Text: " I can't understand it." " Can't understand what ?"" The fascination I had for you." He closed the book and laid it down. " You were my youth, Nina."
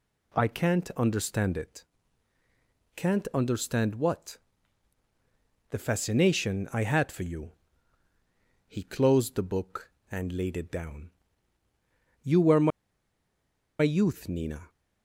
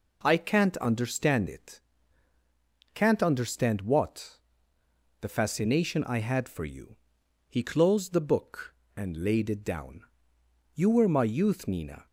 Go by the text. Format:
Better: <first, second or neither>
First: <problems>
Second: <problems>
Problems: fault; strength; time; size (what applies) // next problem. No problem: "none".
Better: second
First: pauses between "my" and "youth"; at 12.7 s; 1.1 s long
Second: none